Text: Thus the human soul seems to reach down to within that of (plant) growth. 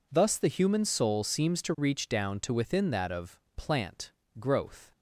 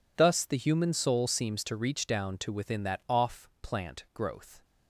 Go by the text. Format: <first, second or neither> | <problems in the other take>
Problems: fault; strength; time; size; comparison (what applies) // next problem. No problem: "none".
first | says "off" for "of"; at 3.0 s